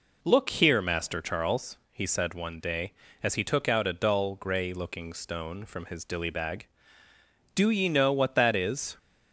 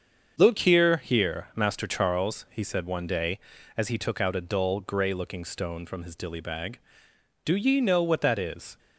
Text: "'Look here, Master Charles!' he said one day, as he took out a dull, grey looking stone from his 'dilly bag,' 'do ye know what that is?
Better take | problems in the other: first | starts louder than the rest; until 1.3 s; 7 dB // says "here" twice; at 0.9 s

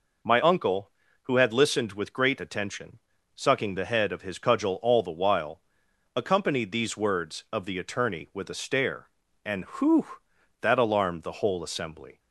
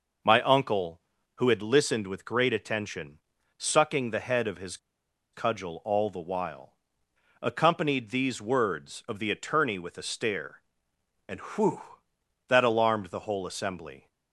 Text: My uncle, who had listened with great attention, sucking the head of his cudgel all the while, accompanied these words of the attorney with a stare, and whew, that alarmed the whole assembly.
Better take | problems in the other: first | pauses between "his" and "cudgel"; noticeable; at 4.7 s; 0.56 s long

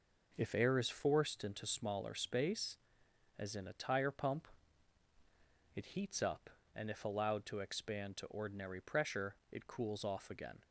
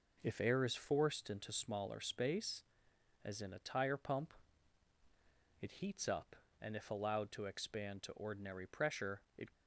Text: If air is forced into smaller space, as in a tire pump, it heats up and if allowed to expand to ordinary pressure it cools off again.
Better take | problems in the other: first | pauses between "pressure" and "it"; slight; at 9.2 s; 0.16 s long; slight in the first // stops before "cools off again"; at 9.5 s

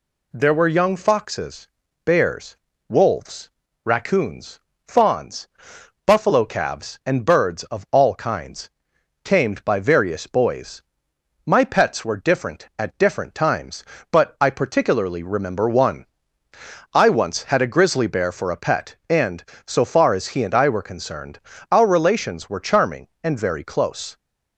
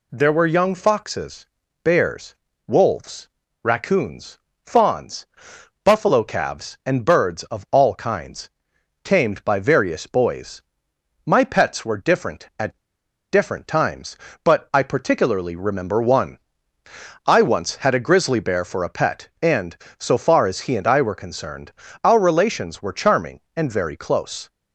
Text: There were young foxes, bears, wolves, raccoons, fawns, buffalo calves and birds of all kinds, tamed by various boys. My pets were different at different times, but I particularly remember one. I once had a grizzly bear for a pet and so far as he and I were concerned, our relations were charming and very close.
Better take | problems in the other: first | pauses between "at" and "different"; noticeable; at 12.7 s; 0.54 s long

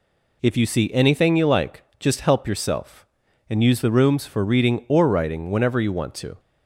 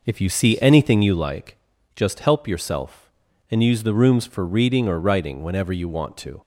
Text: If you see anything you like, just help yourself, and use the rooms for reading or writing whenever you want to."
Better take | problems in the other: first | starts louder than the rest; noticeable; until 1.4 s; 5 dB

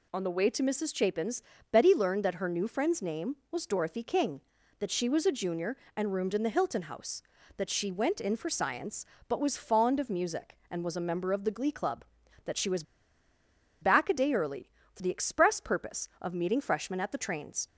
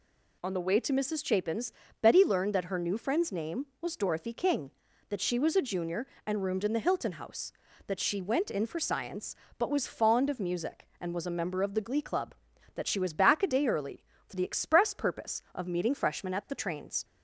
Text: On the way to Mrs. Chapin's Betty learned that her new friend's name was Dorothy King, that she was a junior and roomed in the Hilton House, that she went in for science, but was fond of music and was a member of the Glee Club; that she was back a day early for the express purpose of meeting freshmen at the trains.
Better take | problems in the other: second | pauses between "Chapin's" and "Betty"; slight; at 1.4 s; 0.28 s long; slight in the second // pauses between "was" and "back"; at 12.8 s; 0.99 s long

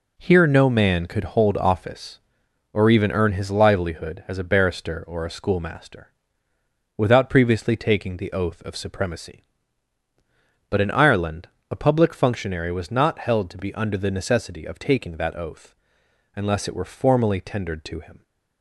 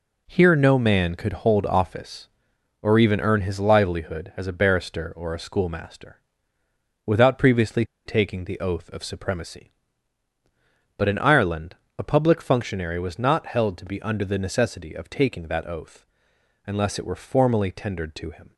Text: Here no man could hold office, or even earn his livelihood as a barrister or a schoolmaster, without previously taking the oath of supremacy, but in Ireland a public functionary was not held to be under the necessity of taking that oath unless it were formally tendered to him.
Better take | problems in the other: first | pauses between "previously" and "taking"; slight; at 7.8 s; 0.20 s long // pauses between "Ireland" and "a"; slight; at 11.7 s; 0.22 s long; slight in the first // pauses between "oath" and "unless"; noticeable; at 16.0 s; 0.60 s long; noticeable in the first

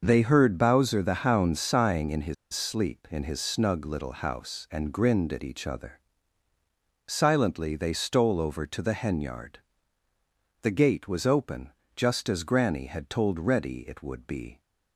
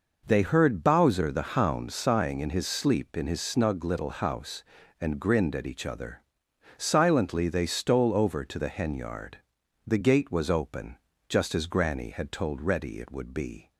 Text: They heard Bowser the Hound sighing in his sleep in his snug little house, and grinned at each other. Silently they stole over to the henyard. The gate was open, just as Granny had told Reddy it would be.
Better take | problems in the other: second | starts louder than the rest; noticeable; until 1.0 s; 6 dB // pauses between "his" and "sleep"; slight; at 2.3 s; 0.19 s long

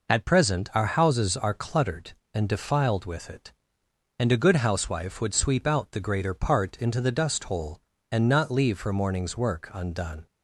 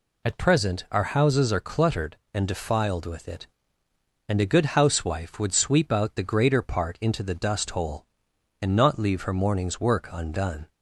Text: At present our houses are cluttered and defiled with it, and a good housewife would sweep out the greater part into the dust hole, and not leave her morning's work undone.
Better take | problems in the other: neither | none

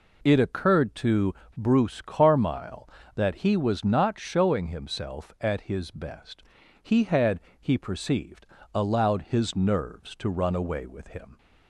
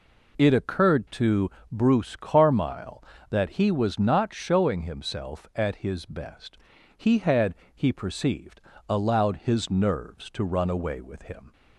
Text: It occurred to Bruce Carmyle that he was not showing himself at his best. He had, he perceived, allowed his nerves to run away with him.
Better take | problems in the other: neither | pauses between "to" and "Bruce"; slight; the same in both

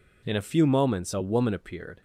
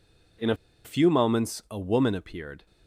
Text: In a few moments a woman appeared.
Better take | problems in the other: first | pauses between "a" and "few"; slight; at 0.5 s; 0.29 s long

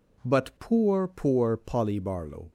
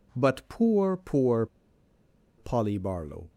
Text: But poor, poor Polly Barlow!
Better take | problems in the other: first | pauses between "poor" and "Polly"; noticeable; at 1.4 s; 0.92 s long

